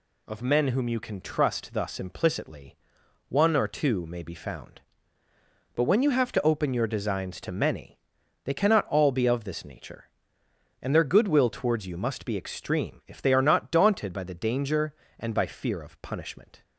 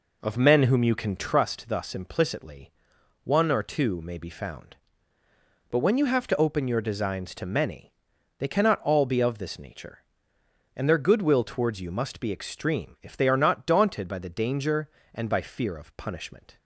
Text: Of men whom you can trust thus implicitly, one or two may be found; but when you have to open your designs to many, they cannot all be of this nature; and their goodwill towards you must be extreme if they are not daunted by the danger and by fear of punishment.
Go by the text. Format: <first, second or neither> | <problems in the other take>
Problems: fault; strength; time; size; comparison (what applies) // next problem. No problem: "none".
first | starts louder than the rest; until 1.4 s; 4 dB